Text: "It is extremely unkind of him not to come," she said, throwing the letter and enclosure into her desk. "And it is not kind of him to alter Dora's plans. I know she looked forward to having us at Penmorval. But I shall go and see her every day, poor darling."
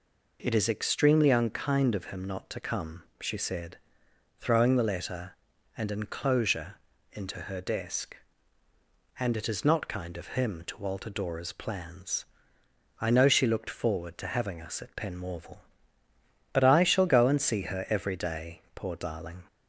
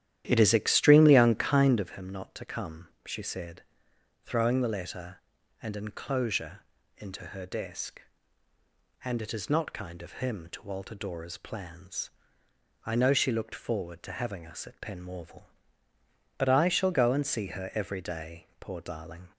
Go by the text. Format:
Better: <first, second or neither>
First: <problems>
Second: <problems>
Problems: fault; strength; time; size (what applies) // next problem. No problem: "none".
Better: first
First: pauses between "enclosure" and "into"; slight; at 6.7 s; 0.34 s long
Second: starts louder than the rest; strong; until 1.9 s; 11.5 dB // pauses between "enclosure" and "into"; slight; at 6.6 s; 0.34 s long